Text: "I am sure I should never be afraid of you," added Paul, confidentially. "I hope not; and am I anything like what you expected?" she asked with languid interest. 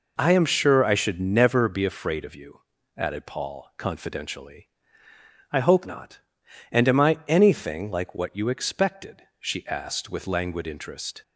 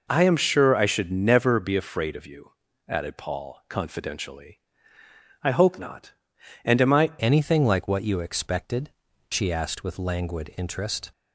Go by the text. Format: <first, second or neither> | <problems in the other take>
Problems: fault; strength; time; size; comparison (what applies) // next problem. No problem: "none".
first | changes voice at "anything"; from 7.1 s on; 4.0 s long